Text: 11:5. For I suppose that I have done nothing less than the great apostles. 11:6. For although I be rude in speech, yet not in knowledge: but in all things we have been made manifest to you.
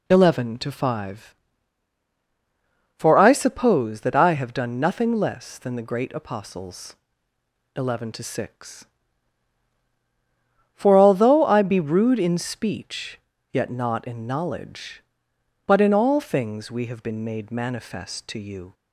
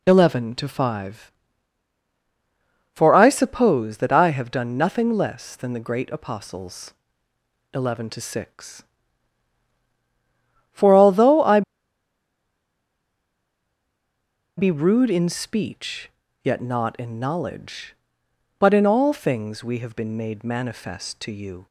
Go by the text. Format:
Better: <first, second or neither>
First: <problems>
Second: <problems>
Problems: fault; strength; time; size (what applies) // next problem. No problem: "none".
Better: first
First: none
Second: pauses between "I" and "be"; strong; at 11.6 s; 2.9 s long